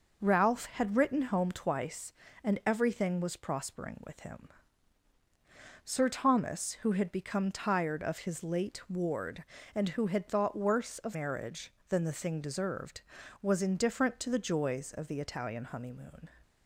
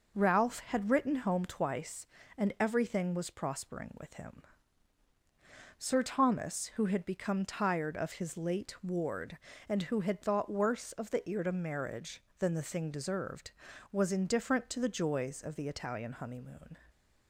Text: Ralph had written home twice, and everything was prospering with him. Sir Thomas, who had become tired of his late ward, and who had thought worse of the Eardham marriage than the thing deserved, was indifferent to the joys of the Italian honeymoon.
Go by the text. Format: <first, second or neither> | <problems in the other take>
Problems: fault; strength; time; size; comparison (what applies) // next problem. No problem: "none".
second | skips "the Eardham"; at 11.1 s